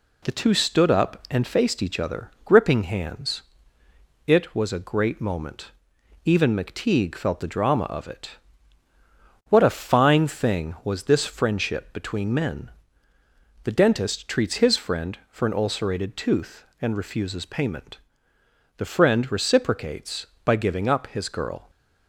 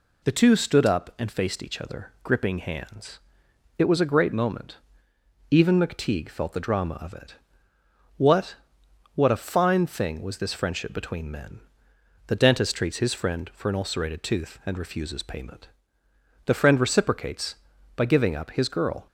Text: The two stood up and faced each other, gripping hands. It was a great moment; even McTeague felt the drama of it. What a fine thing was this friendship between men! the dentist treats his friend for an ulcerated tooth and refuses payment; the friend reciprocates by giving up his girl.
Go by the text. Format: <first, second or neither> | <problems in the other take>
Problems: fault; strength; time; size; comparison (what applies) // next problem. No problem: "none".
first | says "What" twice; at 9.1 s